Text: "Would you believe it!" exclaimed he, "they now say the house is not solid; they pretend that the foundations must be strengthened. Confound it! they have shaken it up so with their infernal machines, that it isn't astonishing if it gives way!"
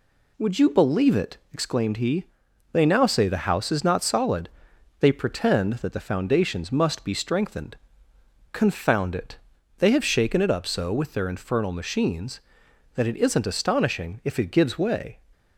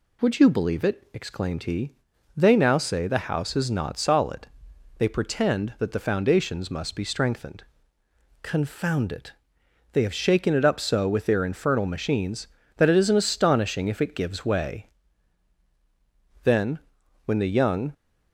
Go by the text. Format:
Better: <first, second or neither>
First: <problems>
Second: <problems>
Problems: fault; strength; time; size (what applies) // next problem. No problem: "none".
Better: first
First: none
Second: goes on to say "Then when the young"; from 16.4 s on; 1.5 s long